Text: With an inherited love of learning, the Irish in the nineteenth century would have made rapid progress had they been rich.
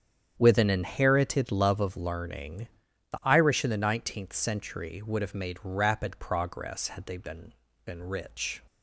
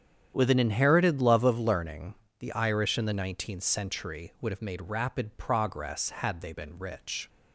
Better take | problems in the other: second | starts louder than the rest; strong; until 1.4 s; 8.5 dB; strong in the second // says "been" twice; at 7.8 s

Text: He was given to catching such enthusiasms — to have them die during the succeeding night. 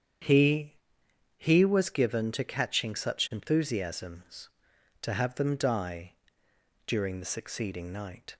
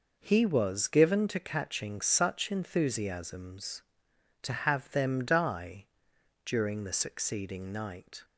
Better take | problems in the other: second | starts louder than the rest; strong; until 1.8 s; 8.5 dB // says "He" twice; at 1.3 s // pauses between "die" and "during"; noticeable; at 6.1 s; 0.74 s long; noticeable in the second

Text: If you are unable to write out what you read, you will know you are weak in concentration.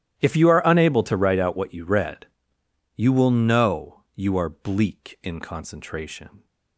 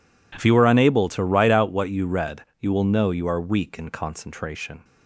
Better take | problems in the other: second | starts louder than the rest; strong; until 1.2 s; 12.5 dB // says "bleak" for "weak"; at 4.4 s

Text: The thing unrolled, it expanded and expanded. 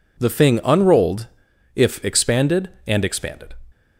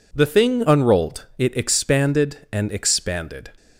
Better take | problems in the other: second | says "if" for "it"; at 1.7 s

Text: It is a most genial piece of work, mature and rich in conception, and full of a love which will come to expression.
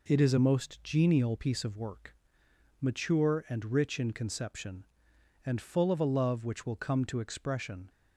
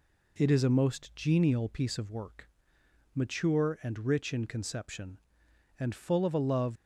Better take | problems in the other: first | stops before "which will come to expression"; at 6.7 s

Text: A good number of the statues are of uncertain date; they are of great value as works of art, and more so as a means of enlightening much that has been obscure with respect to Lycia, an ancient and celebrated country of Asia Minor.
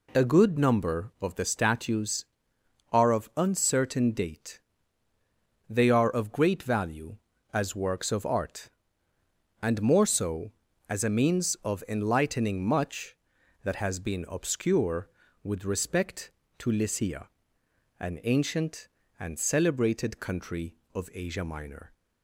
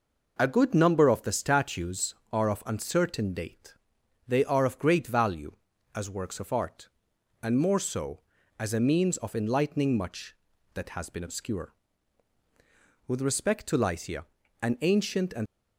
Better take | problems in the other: first | stops before "celebrated country of Asia Minor"; at 15.4 s

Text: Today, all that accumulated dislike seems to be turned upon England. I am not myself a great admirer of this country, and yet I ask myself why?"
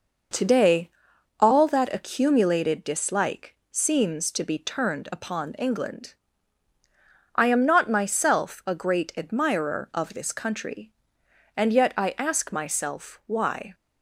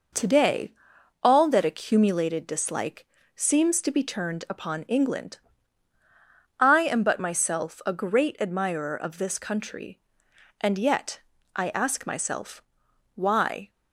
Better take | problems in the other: first | pauses between "dislike" and "seems"; slight; at 3.0 s; 0.30 s long; slight in the first // says "but" for "not"; at 7.0 s // pauses between "yet" and "I"; slight; at 11.1 s; 0.36 s long // pauses between "myself" and "why"; noticeable; at 12.6 s; 0.54 s long

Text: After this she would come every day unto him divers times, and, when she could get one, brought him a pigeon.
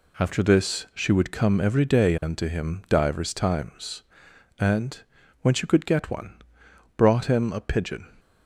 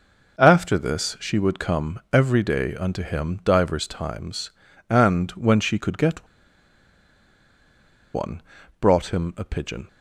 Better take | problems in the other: first | pauses between "get" and "one"; strong; at 6.2 s; 1.8 s long

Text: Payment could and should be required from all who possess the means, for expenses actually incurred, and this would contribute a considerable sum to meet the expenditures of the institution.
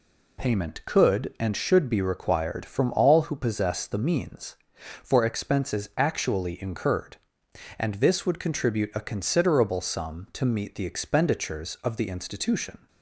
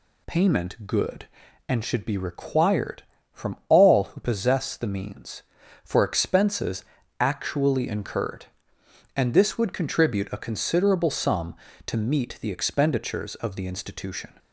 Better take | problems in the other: first | says "good" for "could"; at 0.8 s // pauses between "expenses" and "actually"; slight; at 6.8 s; 0.34 s long

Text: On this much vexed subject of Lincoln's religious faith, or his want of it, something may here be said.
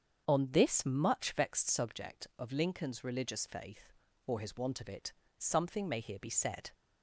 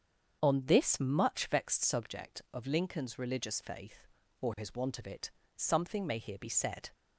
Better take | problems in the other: neither | starts louder than the rest; strong; the same in both

